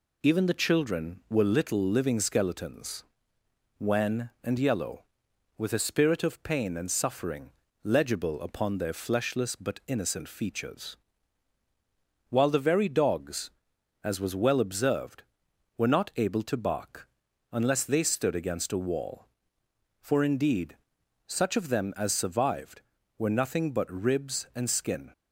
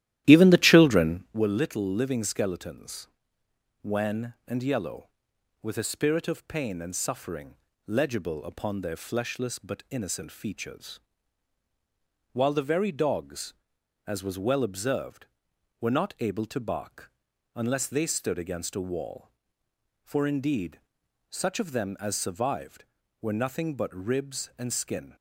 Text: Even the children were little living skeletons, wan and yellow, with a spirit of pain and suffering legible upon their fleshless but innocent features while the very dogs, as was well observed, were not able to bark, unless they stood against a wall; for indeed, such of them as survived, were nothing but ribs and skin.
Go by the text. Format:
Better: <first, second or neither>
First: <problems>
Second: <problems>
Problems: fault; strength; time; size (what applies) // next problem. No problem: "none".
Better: first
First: pauses between "suffering" and "legible"; slight; at 7.5 s; 0.34 s long // pauses between "features" and "while"; strong; at 10.9 s; 1.3 s long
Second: starts louder than the rest; strong; until 1.4 s; 13.5 dB // pauses between "suffering" and "legible"; slight; at 7.5 s; 0.32 s long // pauses between "features" and "while"; strong; at 10.9 s; 1.3 s long